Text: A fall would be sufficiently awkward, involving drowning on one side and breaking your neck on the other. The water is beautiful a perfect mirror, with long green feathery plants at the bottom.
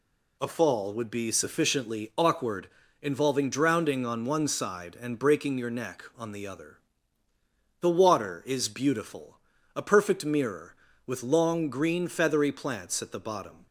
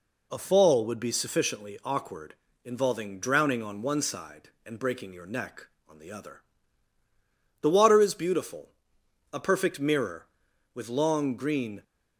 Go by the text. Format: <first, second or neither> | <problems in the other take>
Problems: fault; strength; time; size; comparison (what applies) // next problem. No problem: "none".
first | pauses between "beautiful" and "a"; noticeable; at 8.6 s; 0.64 s long; also in the first // stops before "feathery plants at the bottom"; at 11.8 s